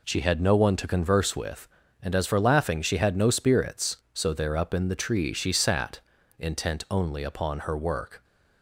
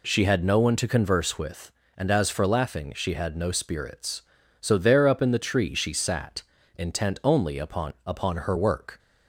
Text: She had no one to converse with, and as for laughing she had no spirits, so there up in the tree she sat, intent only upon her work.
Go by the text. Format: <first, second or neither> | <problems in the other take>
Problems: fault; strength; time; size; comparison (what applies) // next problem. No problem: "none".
first | says "upon" twice; at 8.0 s